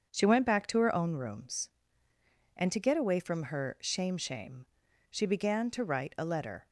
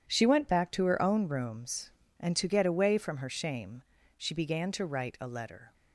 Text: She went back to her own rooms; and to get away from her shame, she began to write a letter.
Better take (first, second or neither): second